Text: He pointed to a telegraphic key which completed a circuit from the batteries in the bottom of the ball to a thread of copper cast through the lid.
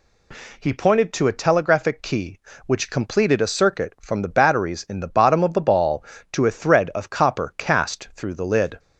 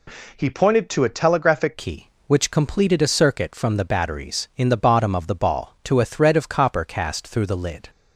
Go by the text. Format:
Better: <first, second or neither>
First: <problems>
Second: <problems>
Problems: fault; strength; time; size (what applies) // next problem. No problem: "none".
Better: first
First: none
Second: changes voice at "key"; from 1.7 s on; 6.1 s long